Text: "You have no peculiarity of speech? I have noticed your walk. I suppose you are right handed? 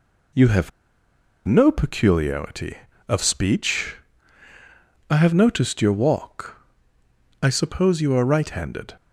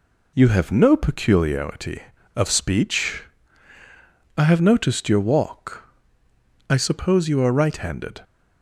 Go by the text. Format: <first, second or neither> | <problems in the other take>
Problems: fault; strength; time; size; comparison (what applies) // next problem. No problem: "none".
second | pauses between "have" and "no"; noticeable; at 0.7 s; 0.75 s long